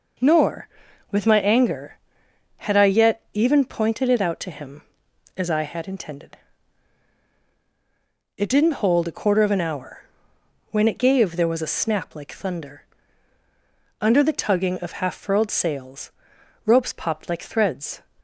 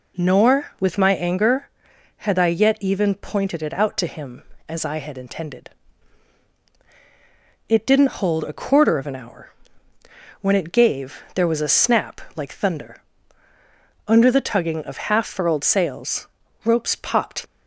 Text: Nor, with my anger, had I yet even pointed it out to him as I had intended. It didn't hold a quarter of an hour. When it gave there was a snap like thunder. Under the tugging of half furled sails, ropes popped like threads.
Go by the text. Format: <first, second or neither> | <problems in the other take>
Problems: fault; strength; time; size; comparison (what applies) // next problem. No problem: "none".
first | pauses between "snap" and "like"; slight; at 12.2 s; 0.16 s long // stops before "like threads"; at 17.4 s